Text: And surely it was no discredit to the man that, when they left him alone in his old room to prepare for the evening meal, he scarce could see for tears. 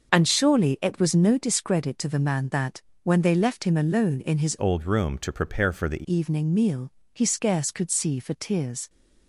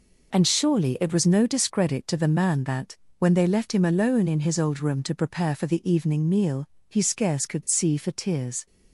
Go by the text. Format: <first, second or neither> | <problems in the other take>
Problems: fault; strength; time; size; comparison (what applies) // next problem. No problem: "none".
second | starts louder than the rest; until 1.1 s; 6.5 dB // changes voice from "old" to "the"; from 4.5 to 6.0 s; 1.5 s long